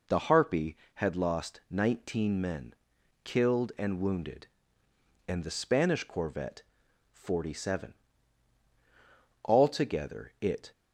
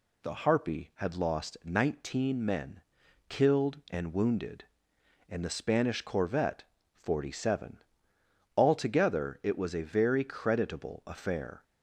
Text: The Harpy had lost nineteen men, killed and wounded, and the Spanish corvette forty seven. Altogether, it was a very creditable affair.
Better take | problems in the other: second | pauses between "corvette" and "forty"; noticeable; at 6.6 s; 0.50 s long; slight in the second // stops before "was a very creditable affair"; at 10.7 s

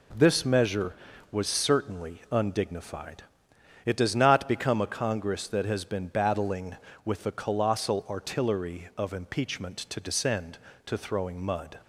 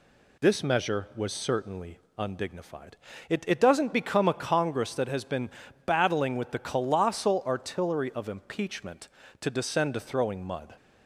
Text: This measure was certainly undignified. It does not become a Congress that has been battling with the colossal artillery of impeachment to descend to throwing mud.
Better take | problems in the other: first | pauses between "certainly" and "undignified"; slight; at 1.9 s; 0.18 s long // says "It" twice; at 3.4 s // pauses between "been" and "battling"; slight; at 5.4 s; 0.36 s long

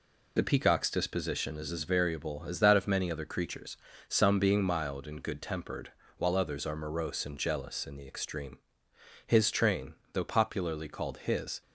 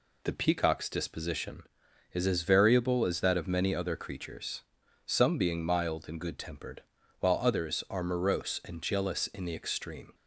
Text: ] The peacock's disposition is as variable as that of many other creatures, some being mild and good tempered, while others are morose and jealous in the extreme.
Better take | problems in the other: second | goes on to say "His train though popularly called his"; strong; from 9.2 s on; 2.3 s long

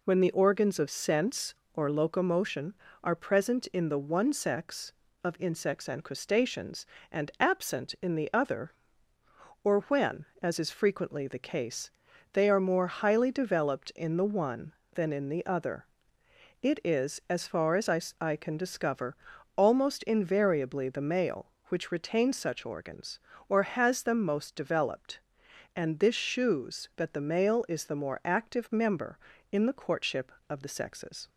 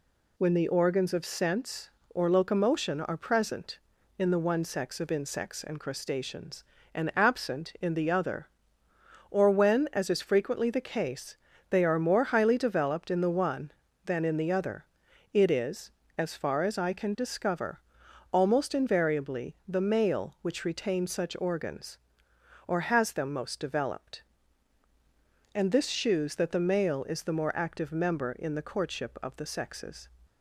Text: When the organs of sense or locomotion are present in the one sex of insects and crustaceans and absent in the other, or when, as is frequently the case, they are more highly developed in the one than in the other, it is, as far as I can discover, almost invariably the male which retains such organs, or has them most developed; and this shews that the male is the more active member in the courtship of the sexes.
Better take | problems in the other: second | says "I" twice; at 18.1 s

